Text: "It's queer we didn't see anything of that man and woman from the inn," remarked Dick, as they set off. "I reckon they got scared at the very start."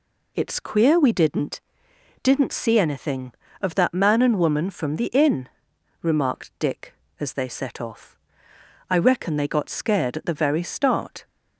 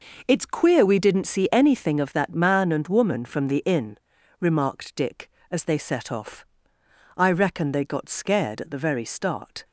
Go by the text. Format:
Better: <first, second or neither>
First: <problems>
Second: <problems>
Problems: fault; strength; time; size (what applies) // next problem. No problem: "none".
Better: second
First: says "didn't" twice; at 2.2 s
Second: none